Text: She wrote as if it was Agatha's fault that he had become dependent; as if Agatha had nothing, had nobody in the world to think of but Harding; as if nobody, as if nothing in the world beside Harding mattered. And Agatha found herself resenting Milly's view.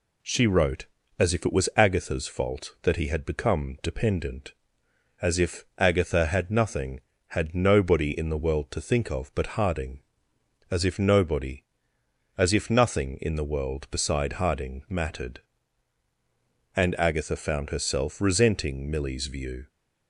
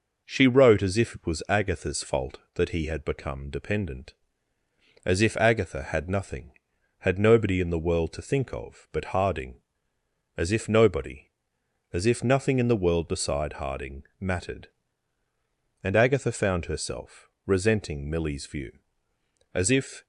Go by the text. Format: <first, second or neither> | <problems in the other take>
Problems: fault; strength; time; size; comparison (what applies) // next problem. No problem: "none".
first | pauses between "Harding" and "mattered"; slight; at 14.0 s; 0.16 s long // pauses between "herself" and "resenting"; slight; at 17.2 s; 0.16 s long // goes on to say "As if"; from 19.5 s on; 0.51 s long